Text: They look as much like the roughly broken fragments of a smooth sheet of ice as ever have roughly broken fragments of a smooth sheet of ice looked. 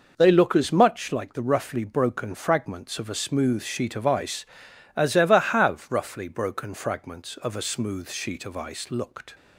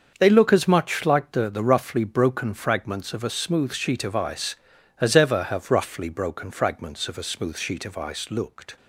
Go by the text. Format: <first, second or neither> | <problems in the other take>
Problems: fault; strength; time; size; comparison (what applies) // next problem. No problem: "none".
first | starts louder than the rest; until 1.2 s; 6.5 dB // says "the" twice; at 1.4 s